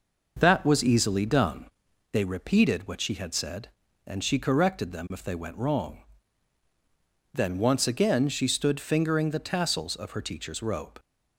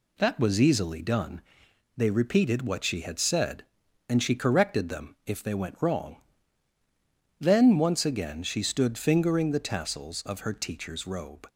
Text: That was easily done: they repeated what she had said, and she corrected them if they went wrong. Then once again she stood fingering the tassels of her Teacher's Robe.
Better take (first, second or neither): neither